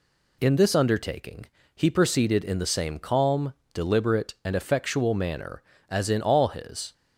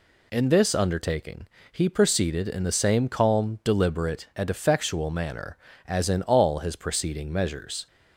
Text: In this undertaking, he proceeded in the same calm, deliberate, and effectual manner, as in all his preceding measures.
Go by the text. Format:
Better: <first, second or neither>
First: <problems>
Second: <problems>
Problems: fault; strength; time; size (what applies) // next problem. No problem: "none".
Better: second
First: stops before "preceding measures"; at 6.9 s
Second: none